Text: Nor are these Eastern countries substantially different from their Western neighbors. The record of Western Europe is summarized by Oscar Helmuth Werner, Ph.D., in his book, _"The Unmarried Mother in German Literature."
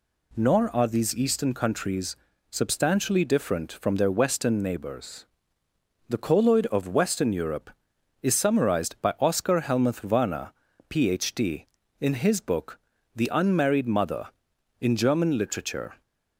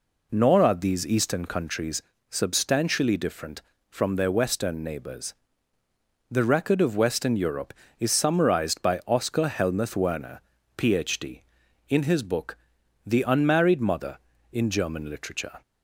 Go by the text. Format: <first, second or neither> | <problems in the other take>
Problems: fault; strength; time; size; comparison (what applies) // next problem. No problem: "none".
second | pauses between "countries" and "substantially"; slight; at 2.1 s; 0.34 s long; slight in the second // says "colloid" for "record"; at 6.1 s